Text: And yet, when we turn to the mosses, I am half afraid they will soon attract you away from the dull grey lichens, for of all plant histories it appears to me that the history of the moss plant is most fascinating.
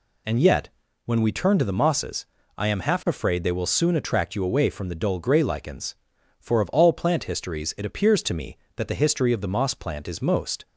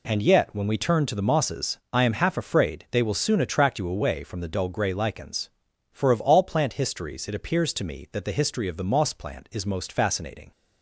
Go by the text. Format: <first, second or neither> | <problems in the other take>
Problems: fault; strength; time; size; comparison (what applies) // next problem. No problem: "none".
second | stops before "fascinating"; at 10.6 s